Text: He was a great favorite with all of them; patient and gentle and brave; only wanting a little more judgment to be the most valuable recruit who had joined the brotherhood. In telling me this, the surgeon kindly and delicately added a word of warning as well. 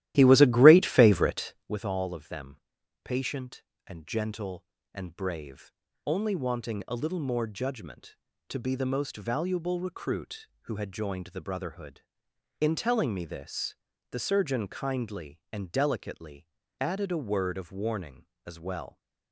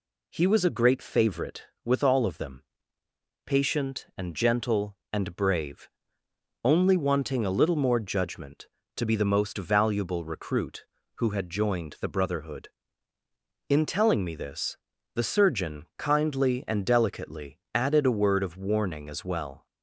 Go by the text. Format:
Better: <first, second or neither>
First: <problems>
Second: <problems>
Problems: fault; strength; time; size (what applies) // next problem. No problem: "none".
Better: second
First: starts louder than the rest; strong; until 1.8 s; 14 dB // pauses between "delicately" and "added"; slight; at 16.4 s; 0.34 s long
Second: pauses between "delicately" and "added"; slight; at 17.5 s; 0.16 s long